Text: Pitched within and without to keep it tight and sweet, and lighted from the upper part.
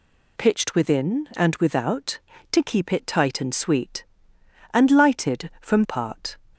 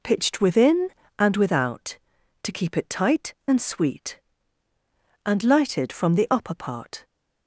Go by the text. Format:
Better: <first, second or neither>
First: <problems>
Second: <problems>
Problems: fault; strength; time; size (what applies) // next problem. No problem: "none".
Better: second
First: skips "the upper"; at 5.8 s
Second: none